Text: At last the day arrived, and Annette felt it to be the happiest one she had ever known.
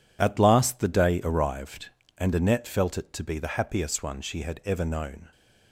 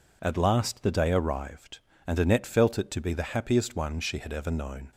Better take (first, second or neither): second